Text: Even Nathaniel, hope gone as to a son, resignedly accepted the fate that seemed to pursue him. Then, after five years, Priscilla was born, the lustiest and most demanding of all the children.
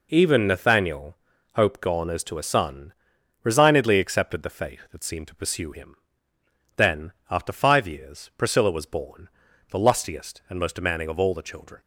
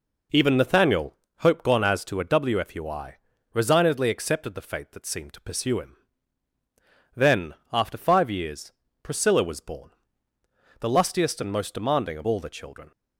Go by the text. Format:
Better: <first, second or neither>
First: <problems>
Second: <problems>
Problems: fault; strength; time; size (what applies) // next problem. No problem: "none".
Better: first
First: none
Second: says "wfui" for "son"; at 2.2 s